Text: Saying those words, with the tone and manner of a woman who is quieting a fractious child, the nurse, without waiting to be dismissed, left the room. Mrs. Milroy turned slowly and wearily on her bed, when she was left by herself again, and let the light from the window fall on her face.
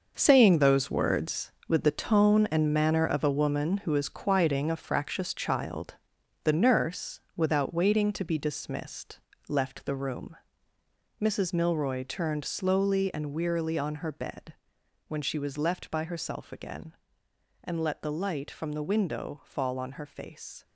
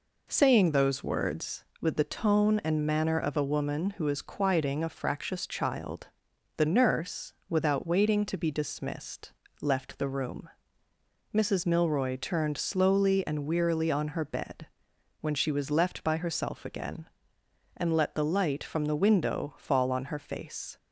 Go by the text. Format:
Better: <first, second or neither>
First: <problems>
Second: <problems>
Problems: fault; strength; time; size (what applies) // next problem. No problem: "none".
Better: second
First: gets quieter; strong; throughout; 10.5 dB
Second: none